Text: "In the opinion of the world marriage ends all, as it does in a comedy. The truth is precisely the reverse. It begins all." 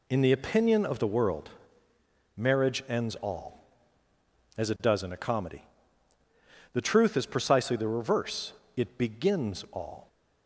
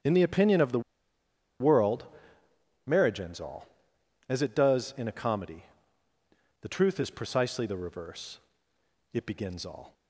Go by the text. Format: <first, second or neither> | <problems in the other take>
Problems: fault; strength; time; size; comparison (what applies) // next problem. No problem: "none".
first | starts louder than the rest; strong; until 1.8 s; 8.5 dB // pauses between "the" and "world"; noticeable; at 0.7 s; 0.80 s long // pauses between "world" and "marriage"; noticeable; at 2.0 s; 0.80 s long; noticeable in the first